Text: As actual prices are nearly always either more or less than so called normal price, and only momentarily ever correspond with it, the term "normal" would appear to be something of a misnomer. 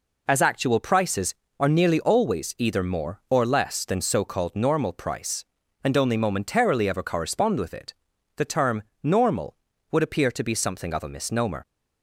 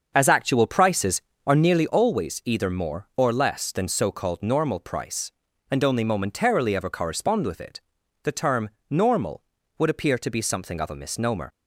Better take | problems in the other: first | starts louder than the rest; until 1.7 s; 6.5 dB // pauses between "term" and "normal"; slight; at 8.6 s; 0.22 s long; slight in the first

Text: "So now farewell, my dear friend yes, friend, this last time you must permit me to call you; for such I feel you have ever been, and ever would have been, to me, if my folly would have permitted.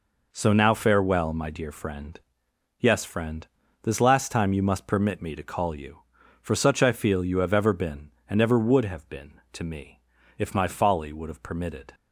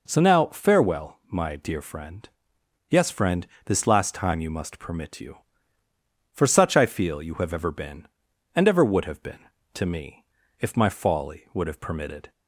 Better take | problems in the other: first | pauses between "friend" and "yes"; noticeable; at 2.2 s; 0.60 s long; noticeable in the first // skips "me to call"; at 5.2 s

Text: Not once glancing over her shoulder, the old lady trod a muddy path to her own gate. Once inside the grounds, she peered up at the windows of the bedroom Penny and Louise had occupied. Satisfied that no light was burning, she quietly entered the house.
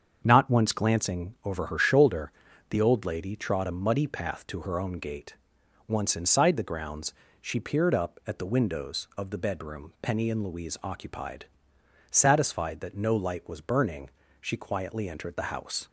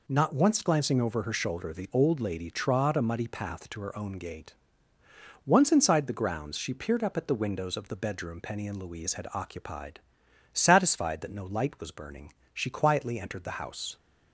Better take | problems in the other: second | starts louder than the rest; until 1.2 s; 7 dB // skips "had"; at 10.8 s

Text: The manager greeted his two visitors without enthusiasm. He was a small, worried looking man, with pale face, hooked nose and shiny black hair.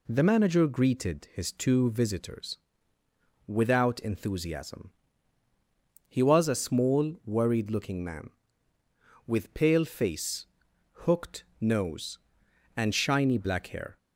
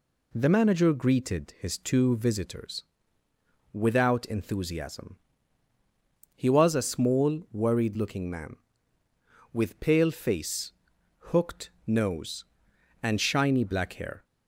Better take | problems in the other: neither | pauses between "visitors" and "without"; noticeable; the same in both // pauses between "hooked" and "nose"; slight; the same in both

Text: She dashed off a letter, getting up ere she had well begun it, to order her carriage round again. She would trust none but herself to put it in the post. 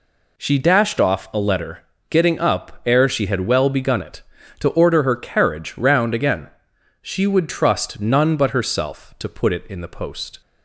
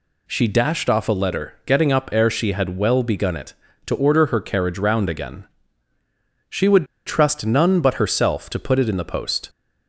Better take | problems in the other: first | pauses between "would" and "trust"; slight; at 6.8 s; 0.21 s long

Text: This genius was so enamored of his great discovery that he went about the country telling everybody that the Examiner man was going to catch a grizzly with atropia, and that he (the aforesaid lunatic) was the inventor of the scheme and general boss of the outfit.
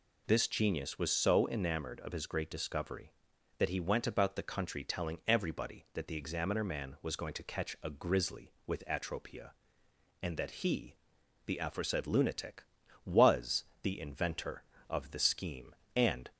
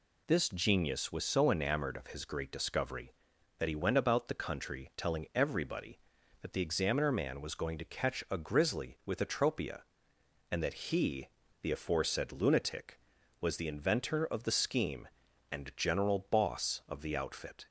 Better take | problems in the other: second | pauses between "was" and "the"; slight; at 13.6 s; 0.18 s long // stops before "general boss of the outfit"; at 16.3 s

